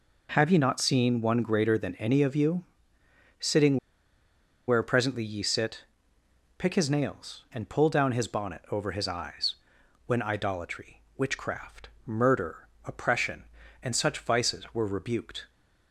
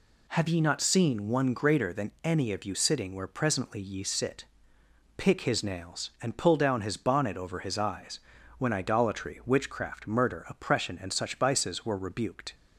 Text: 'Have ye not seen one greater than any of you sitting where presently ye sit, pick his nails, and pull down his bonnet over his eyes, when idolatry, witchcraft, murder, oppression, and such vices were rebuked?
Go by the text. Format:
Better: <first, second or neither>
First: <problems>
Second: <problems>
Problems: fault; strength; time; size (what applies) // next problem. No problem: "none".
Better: second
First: pauses between "you" and "sitting"; noticeable; at 2.6 s; 0.76 s long // pauses between "sitting" and "where"; noticeable; at 3.7 s; 0.91 s long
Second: none